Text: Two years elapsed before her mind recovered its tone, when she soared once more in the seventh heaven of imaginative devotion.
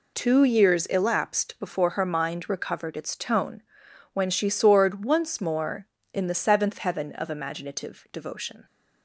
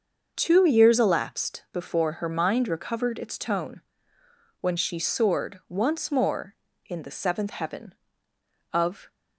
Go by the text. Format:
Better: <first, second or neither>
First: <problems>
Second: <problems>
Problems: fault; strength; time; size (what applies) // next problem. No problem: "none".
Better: first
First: none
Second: starts louder than the rest; until 1.3 s; 6 dB // stops before "imaginative devotion"; at 9.1 s